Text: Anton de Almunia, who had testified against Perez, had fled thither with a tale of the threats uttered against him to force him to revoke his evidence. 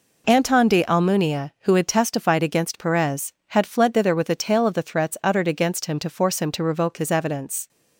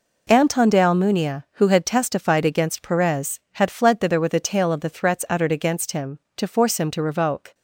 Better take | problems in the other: first | stops before "his evidence"; at 7.5 s

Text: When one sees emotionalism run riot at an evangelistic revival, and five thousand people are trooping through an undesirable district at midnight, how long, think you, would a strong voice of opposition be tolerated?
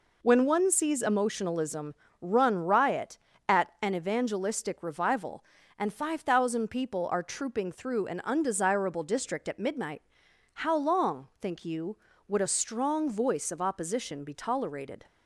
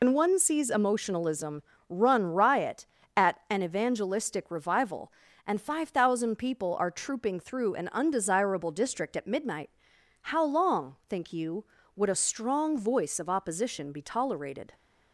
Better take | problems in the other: first | loses the start of "When"; at 0.0 s; 110 ms // pauses between "emotionalism" and "run"; slight; at 1.6 s; 0.26 s long; slight in the first

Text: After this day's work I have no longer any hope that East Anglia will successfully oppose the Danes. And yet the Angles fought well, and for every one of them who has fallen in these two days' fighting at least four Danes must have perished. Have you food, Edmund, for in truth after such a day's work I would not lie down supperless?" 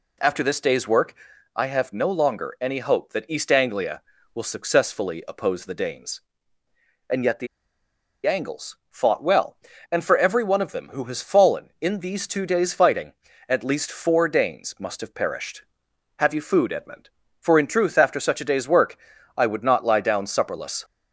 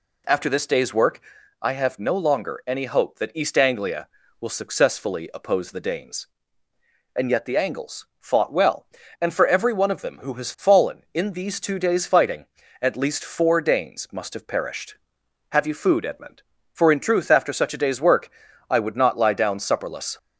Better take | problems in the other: second | pauses between "work" and "I"; at 1.1 s; 0.42 s long; also in the second // pauses between "the" and "Angles"; noticeable; at 7.4 s; 0.79 s long // pauses between "work" and "I"; at 18.9 s; 0.40 s long; also in the second

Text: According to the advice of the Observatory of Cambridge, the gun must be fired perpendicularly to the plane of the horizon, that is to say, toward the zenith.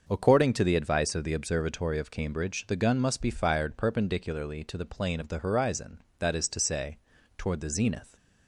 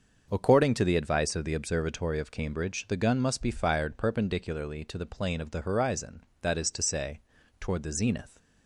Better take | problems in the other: neither | starts louder than the rest; the same in both

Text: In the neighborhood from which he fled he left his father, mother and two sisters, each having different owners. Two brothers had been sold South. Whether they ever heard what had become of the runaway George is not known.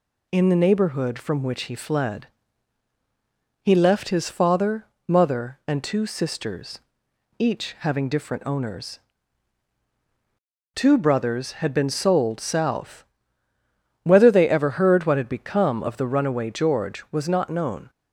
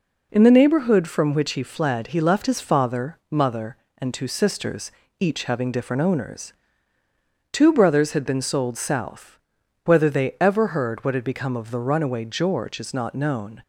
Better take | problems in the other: second | pauses between "fled" and "he"; strong; at 2.2 s; 1.3 s long // says "was" for "is"; at 17.0 s

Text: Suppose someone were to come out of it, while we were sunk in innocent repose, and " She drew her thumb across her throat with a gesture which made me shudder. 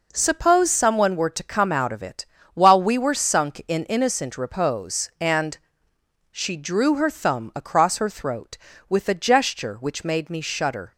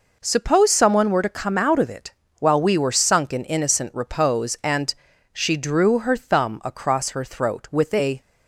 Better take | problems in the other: first | stops before "gesture which made me shudder"; at 8.2 s

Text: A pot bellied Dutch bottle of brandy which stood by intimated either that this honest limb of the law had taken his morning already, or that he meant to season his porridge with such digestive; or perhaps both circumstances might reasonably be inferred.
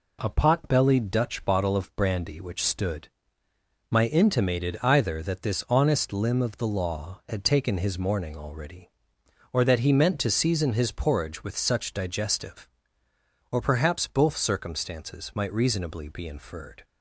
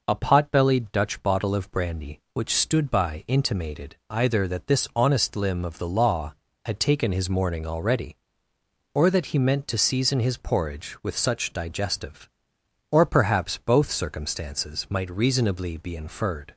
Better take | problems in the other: second | says "my" for "by"; at 3.8 s

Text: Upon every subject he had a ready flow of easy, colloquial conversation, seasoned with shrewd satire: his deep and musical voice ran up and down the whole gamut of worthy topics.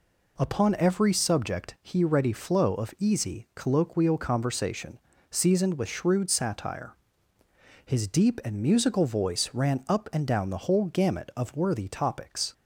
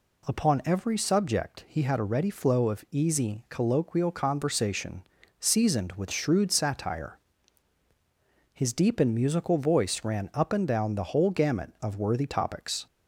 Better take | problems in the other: second | skips "had a"; at 2.0 s

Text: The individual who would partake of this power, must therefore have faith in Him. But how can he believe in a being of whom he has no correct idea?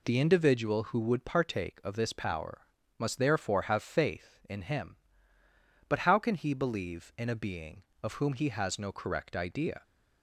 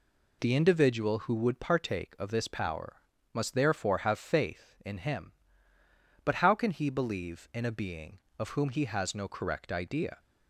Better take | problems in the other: neither | none

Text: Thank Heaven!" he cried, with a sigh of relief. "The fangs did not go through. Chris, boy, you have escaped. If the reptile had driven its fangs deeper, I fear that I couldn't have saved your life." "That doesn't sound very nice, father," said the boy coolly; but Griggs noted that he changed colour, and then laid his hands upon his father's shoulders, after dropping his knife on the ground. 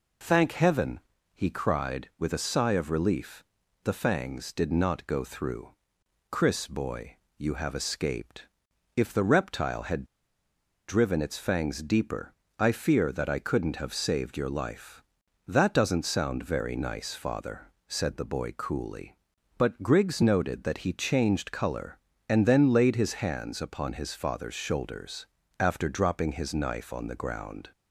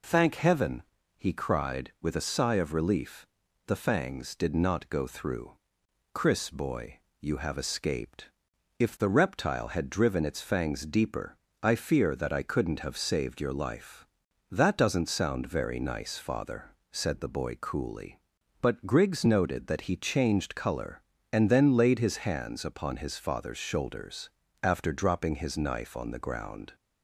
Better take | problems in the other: second | pauses between "had" and "driven"; noticeable; at 10.0 s; 0.84 s long

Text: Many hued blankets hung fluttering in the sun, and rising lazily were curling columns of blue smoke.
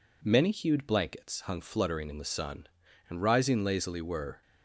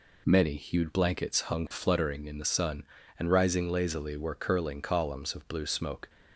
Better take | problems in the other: second | stops before "curling columns of blue smoke"; at 4.4 s

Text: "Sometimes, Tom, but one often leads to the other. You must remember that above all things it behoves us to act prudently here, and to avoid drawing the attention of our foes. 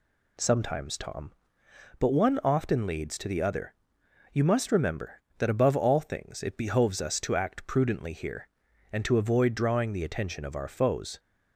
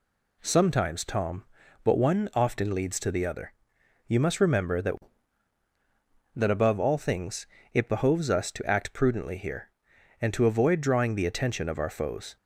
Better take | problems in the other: first | says "that" twice; at 6.3 s // pauses between "things" and "it"; slight; at 7.4 s; 0.28 s long

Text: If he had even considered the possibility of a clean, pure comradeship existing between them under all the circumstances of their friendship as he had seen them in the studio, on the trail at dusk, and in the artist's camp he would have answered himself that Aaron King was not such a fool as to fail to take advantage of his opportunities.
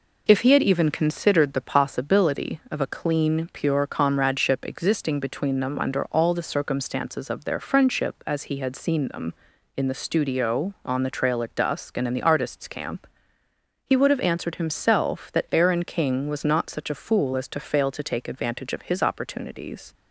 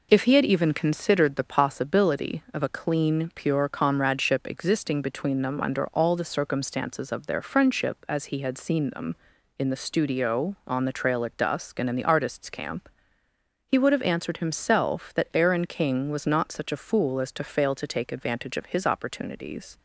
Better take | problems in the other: neither | pauses between "camp" and "he"; noticeable; the same in both

